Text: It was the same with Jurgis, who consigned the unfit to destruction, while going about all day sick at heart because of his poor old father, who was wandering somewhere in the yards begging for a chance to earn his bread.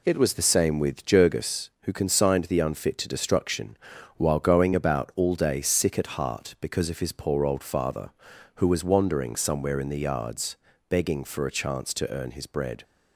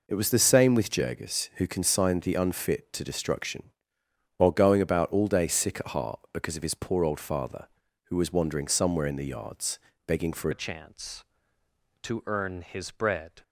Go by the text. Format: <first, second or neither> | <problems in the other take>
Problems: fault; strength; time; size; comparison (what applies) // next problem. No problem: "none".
first | pauses between "yards" and "begging"; slight; at 9.7 s; 0.26 s long; slight in the first // changes voice at "a"; from 10.5 s on; 2.9 s long